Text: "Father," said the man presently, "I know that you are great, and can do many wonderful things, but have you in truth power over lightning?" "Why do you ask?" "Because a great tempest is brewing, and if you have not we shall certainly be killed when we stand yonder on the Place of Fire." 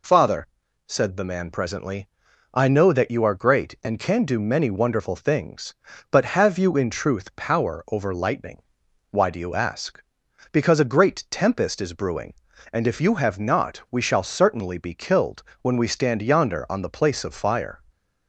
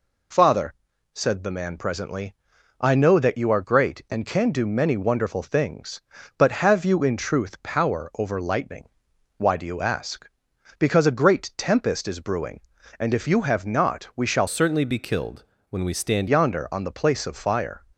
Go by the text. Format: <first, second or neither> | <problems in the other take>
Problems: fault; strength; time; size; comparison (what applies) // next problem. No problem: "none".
first | changes voice from "certainly" to "stand"; from 14.4 to 16.2 s; 1.8 s long // pauses between "killed" and "when"; slight; at 15.4 s; 0.26 s long; slight in the first